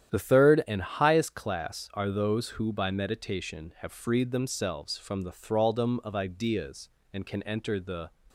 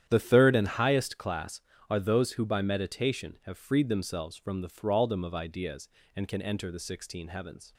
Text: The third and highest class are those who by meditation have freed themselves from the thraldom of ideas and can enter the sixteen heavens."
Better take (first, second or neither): second